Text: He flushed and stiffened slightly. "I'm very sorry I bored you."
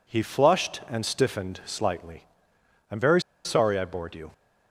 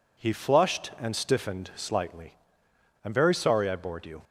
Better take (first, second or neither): second